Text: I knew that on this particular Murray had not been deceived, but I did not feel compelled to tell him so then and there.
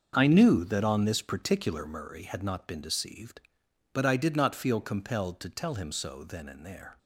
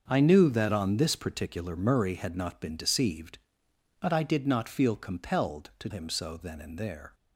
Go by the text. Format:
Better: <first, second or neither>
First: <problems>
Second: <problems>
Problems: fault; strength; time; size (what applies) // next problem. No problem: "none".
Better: first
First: starts louder than the rest; until 1.2 s; 6.5 dB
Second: starts louder than the rest; until 1.1 s; 7 dB // skips "tell"; at 5.8 s